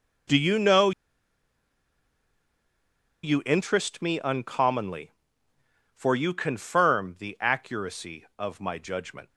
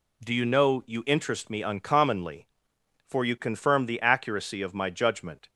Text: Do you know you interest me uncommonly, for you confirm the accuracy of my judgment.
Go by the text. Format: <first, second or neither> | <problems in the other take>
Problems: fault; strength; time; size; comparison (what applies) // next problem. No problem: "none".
second | pauses between "know" and "you"; strong; at 0.9 s; 2.3 s long